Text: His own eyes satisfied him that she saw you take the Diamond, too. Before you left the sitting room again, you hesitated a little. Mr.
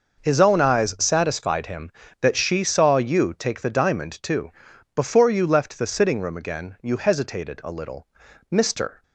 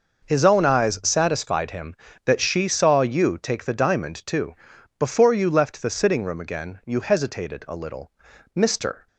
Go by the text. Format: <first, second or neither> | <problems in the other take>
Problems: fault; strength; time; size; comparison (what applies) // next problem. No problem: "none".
neither | none